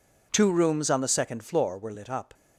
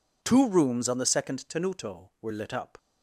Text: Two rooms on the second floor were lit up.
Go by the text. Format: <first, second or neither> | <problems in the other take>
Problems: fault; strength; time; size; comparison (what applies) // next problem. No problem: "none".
first | says "tenuto" for "floor"; at 1.4 s